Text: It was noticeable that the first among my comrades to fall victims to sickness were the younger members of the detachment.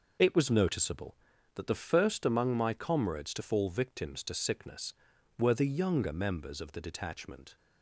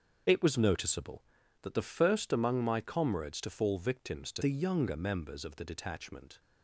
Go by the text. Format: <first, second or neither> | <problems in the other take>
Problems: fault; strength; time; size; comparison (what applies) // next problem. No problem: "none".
first | starts louder than the rest; until 1.6 s; 7 dB // skips "sickness were"; at 4.4 s